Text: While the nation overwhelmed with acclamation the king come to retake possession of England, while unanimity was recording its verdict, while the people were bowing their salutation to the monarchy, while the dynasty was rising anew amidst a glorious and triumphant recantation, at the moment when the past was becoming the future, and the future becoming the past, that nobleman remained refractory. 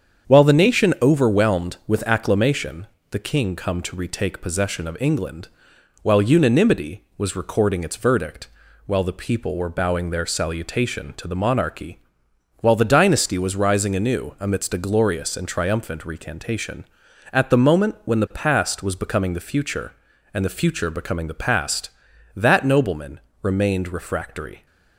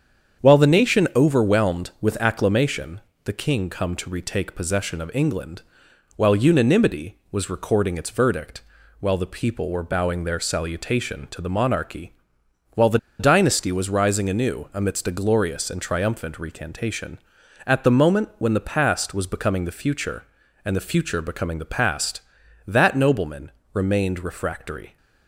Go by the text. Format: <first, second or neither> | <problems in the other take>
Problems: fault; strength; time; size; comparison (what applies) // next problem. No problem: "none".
first | starts louder than the rest; strong; until 1.4 s; 7.5 dB; strong in the first // pauses between "acclamation" and "the"; slight; at 3.0 s; 0.24 s long; slight in the first // pauses between "the" and "dynasty"; slight; at 12.9 s; 0.22 s long // pauses between "nobleman" and "remained"; slight; at 23.5 s; 0.22 s long; slight in the first